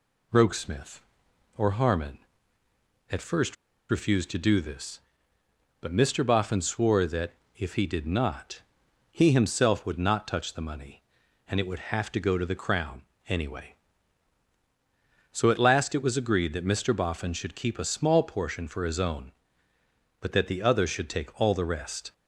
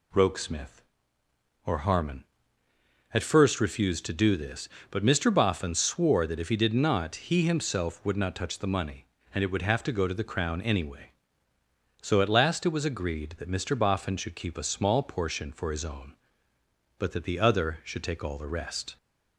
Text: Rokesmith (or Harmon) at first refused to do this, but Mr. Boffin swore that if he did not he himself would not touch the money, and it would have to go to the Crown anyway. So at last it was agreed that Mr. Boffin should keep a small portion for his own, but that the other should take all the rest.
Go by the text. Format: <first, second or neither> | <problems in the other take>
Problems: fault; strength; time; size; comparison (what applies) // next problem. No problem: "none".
second | pauses between "first" and "refused"; slight; at 3.5 s; 0.35 s long // pauses between "that" and "if"; slight; at 7.3 s; 0.24 s long // pauses between "not" and "he"; noticeable; at 8.6 s; 0.50 s long // pauses between "Crown" and "anyway"; slight; at 13.0 s; 0.24 s long